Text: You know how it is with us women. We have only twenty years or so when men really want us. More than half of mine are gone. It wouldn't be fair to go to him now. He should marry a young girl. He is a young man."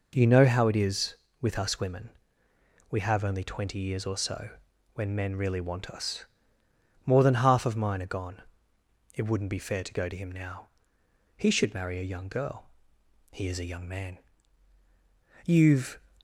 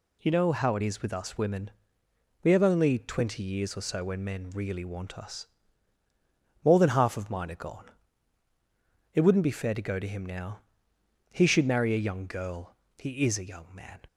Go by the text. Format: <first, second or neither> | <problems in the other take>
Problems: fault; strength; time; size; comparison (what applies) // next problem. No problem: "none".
second | pauses between "so" and "when"; at 4.4 s; 0.44 s long // goes on to say "You've"; from 15.4 s on; 0.52 s long